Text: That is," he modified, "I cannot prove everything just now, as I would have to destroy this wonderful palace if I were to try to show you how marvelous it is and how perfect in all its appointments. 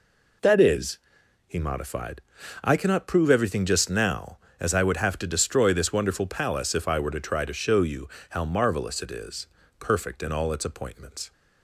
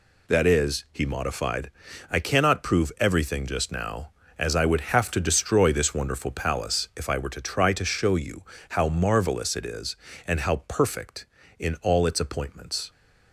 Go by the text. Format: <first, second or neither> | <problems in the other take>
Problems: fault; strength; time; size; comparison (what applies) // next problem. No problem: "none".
second | pauses between "you" and "how"; slight; at 8.0 s; 0.22 s long; slight in the second // skips "and how"; at 9.6 s